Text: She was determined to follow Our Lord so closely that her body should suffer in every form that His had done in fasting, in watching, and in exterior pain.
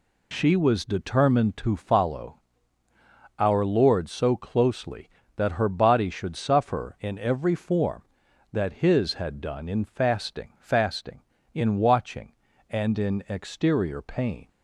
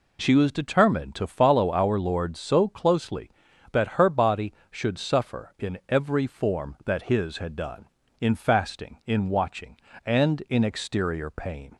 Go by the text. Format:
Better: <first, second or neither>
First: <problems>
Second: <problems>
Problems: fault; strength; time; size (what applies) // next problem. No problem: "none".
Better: second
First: pauses between "follow" and "Our"; noticeable; at 2.3 s; 0.98 s long // says "fasting" twice; at 10.5 s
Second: none